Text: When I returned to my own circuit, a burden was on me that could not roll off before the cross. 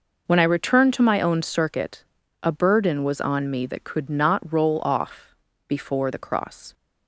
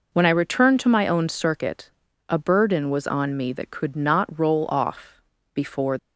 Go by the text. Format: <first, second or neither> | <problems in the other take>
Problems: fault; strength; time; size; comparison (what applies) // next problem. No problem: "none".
first | pauses between "off" and "before"; slight; at 5.2 s; 0.32 s long; slight in the first // stops before "the cross"; at 5.9 s